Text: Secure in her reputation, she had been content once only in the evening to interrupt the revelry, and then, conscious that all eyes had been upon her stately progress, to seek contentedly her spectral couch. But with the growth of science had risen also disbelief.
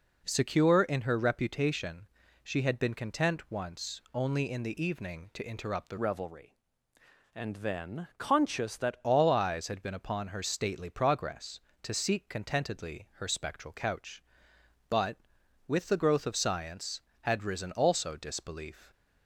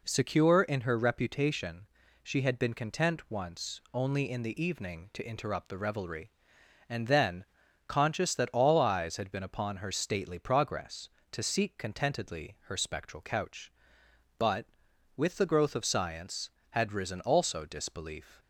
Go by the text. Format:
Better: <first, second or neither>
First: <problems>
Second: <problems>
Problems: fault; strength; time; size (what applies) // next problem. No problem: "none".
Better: second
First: changes voice from "revelry" to "that"; from 5.9 to 9.0 s; 3.1 s long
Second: none